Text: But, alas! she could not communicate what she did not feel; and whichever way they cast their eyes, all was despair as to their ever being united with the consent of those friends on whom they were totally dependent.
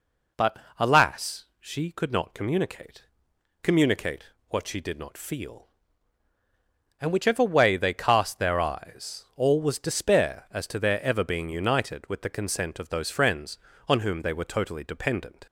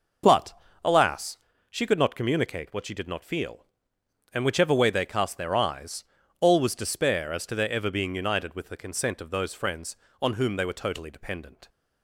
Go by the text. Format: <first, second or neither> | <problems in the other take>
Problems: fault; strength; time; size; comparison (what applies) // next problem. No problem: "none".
second | says "communicate" twice; at 3.6 s